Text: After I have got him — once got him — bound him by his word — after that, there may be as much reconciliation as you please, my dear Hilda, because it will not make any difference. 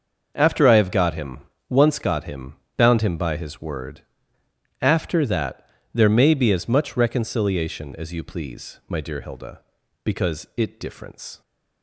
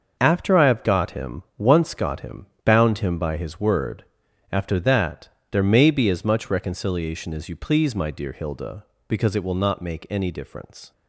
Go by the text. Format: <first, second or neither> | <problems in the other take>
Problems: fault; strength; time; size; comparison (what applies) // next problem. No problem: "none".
second | starts louder than the rest; until 1.3 s; 6 dB; also in the second // skips "will not make any"; at 10.7 s